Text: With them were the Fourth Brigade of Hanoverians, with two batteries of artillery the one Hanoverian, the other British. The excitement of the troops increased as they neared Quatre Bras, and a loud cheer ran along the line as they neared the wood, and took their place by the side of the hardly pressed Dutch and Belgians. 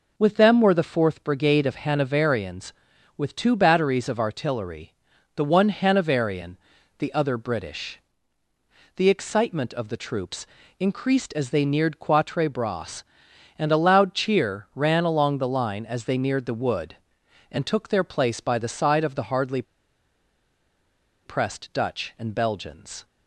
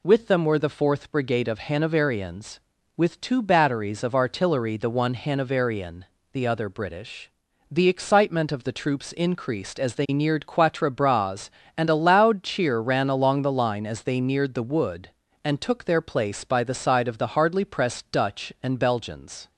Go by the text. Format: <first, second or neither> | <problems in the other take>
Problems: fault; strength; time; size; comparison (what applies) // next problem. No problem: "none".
second | pauses between "artillery" and "the"; at 4.9 s; 0.44 s long // pauses between "troops" and "increased"; slight; at 10.4 s; 0.32 s long // pauses between "hardly" and "pressed"; strong; at 19.6 s; 1.6 s long